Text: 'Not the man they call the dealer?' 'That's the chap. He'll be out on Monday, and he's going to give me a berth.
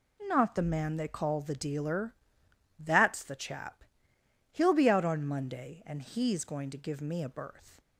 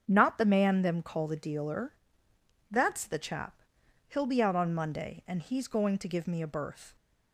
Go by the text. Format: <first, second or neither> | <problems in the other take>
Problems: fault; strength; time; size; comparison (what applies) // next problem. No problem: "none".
first | starts louder than the rest; strong; until 1.0 s; 7.5 dB // says "them" for "they"; at 0.8 s